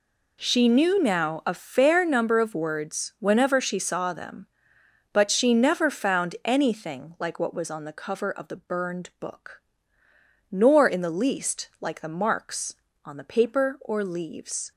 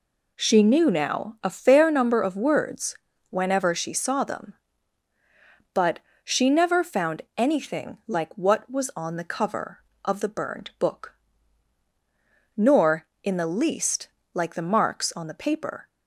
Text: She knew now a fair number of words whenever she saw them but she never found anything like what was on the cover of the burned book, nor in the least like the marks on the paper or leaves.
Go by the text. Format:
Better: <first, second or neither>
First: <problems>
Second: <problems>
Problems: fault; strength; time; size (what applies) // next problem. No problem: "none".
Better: first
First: none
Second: pauses between "words" and "whenever"; slight; at 2.9 s; 0.34 s long // pauses between "but" and "she"; slight; at 5.9 s; 0.26 s long // pauses between "least" and "like"; slight; at 14.0 s; 0.28 s long // stops before "or leaves"; at 15.8 s